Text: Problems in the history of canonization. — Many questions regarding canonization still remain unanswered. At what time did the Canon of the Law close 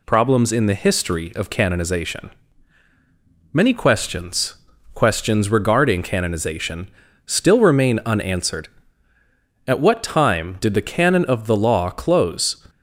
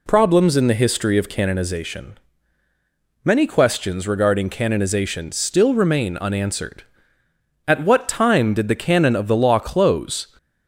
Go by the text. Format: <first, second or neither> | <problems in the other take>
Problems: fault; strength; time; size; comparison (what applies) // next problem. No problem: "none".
second | says "questions" twice; at 4.9 s // pauses between "canonization" and "still"; at 6.8 s; 0.38 s long